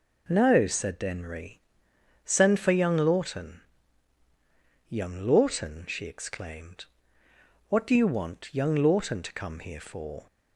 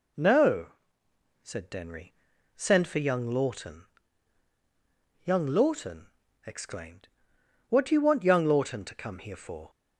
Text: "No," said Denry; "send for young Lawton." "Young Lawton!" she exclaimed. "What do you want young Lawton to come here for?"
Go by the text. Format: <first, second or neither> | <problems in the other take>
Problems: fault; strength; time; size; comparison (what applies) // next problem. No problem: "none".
first | skips "she"; at 6.2 s